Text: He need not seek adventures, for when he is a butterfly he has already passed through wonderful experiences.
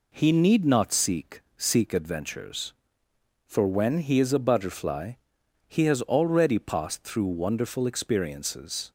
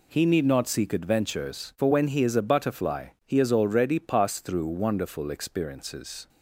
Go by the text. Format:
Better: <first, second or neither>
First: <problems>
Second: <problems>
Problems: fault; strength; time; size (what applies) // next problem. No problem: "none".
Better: second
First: says "seek" twice; at 1.5 s // pauses between "butterfly" and "he"; noticeable; at 5.1 s; 0.54 s long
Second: pauses between "butterfly" and "he"; slight; at 3.0 s; 0.18 s long